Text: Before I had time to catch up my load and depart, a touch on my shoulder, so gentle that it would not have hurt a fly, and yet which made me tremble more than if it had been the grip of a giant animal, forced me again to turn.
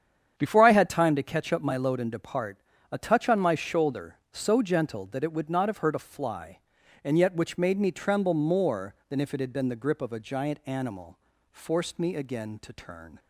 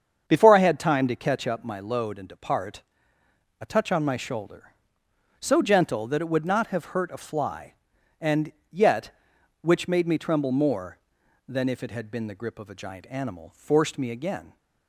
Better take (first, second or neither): first